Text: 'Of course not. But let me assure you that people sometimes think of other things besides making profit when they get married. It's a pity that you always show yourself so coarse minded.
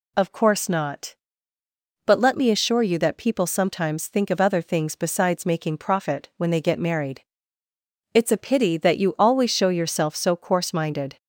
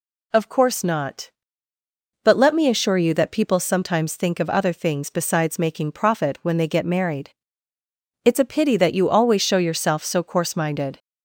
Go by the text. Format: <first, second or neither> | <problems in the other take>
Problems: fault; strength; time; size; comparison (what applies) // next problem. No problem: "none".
neither | none